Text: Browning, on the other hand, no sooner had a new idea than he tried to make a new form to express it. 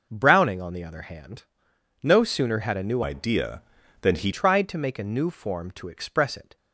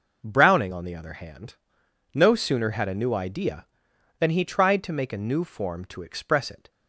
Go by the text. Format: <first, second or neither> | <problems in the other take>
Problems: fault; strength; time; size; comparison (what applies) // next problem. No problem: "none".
second | changes voice from "idea" to "he"; from 3.0 to 4.3 s; 1.3 s long